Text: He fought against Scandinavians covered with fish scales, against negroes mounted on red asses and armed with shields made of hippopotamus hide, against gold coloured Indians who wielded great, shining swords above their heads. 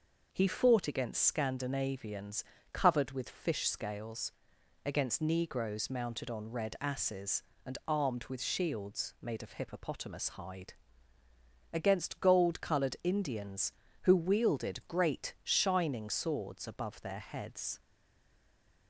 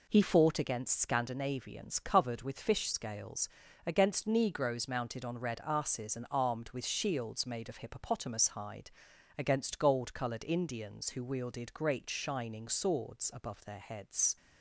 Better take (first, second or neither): second